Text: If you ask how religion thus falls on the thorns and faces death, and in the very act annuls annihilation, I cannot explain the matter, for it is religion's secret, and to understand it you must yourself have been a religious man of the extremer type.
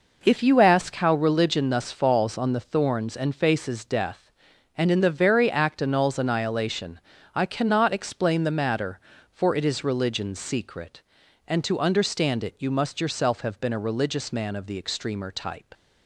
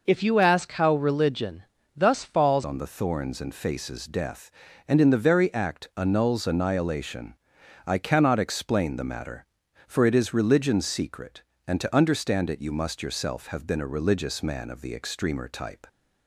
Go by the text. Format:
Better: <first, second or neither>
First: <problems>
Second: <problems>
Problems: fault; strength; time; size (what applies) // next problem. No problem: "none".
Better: first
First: none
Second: pauses between "religion" and "thus"; slight; at 1.6 s; 0.32 s long // changes voice at "on"; from 2.6 s on; 13.2 s long